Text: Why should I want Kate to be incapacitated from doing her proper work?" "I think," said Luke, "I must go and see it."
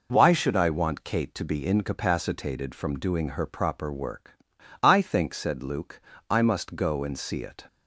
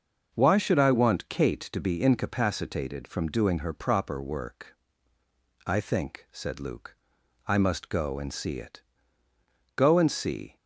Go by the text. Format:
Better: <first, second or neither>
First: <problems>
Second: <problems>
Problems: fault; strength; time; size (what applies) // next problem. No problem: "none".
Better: first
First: none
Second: starts louder than the rest; noticeable; until 1.3 s; 6 dB // goes on to say "Go and see"; noticeable; from 9.7 s on; 0.80 s long